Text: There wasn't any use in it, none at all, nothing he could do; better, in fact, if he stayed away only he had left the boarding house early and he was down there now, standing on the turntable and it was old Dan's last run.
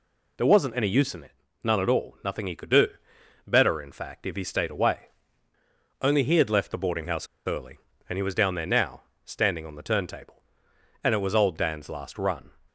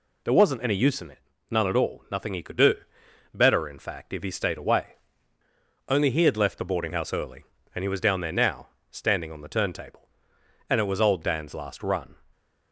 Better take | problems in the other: second | pauses between "away" and "only"; noticeable; at 5.0 s; 0.92 s long; noticeable in the second // pauses between "house" and "early"; slight; at 7.2 s; 0.21 s long

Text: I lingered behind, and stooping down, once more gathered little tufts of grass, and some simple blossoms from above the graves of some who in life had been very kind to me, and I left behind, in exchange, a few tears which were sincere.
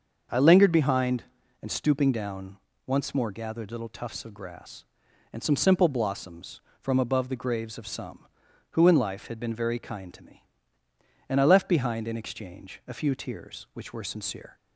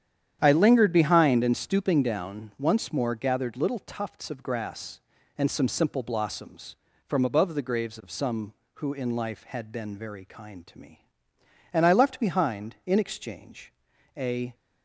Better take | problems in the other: first | starts louder than the rest; strong; until 1.4 s; 9.5 dB; also in the first // stops before "few tears which were sincere"; at 14.5 s

